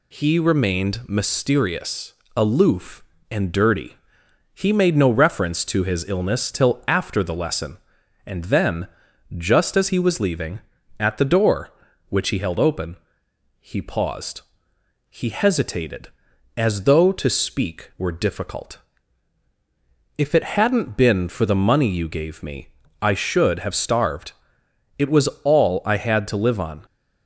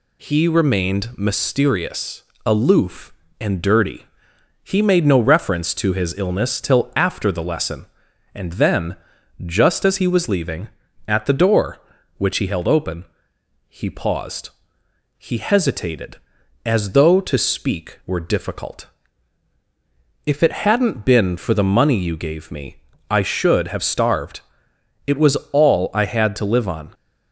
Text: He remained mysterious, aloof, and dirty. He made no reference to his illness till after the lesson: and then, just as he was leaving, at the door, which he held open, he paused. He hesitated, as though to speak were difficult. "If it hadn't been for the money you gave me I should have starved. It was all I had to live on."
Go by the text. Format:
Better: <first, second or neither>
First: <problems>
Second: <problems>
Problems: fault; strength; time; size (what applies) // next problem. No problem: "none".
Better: neither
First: pauses between "me" and "I"; slight; at 22.6 s; 0.34 s long // pauses between "was" and "all"; slight; at 25.2 s; 0.16 s long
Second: pauses between "me" and "I"; slight; at 22.7 s; 0.34 s long // pauses between "was" and "all"; slight; at 25.3 s; 0.16 s long